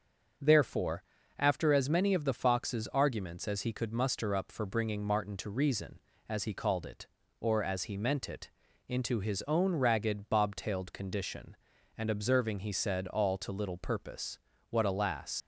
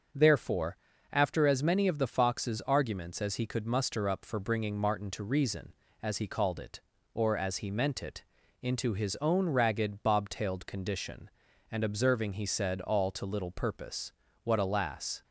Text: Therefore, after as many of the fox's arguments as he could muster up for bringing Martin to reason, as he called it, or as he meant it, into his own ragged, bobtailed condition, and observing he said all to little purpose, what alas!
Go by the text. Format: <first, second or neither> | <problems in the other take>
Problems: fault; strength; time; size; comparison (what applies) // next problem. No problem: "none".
second | starts louder than the rest; until 1.7 s; 7 dB; also in the second // leaves "alas" unfinished; at 15.4 s; 95 ms